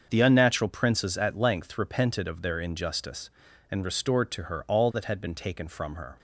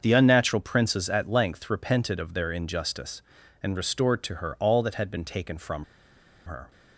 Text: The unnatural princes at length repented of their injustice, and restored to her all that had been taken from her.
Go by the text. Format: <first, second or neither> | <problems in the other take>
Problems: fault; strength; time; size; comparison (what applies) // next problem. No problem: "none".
first | starts louder than the rest; until 1.0 s; 6.5 dB; also in the first // pauses between "from" and "her"; noticeable; at 5.8 s; 0.63 s long